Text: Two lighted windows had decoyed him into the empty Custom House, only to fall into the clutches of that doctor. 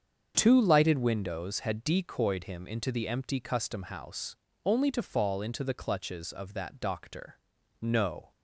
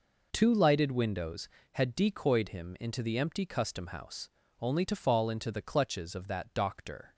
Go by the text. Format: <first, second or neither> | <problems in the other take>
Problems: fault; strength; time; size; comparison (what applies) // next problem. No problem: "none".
second | starts louder than the rest; strong; until 1.3 s; 7 dB // goes on to say "No"; from 7.7 s on; 0.52 s long